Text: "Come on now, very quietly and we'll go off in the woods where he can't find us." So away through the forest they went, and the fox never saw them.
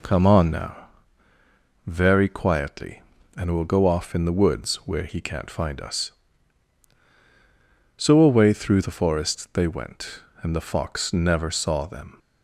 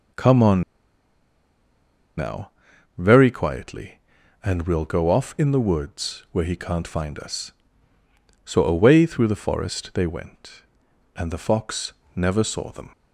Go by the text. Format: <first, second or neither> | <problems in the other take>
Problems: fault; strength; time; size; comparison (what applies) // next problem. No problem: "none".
first | pauses between "on" and "now"; strong; at 0.6 s; 1.5 s long // pauses between "fox" and "never"; slight; at 11.9 s; 0.24 s long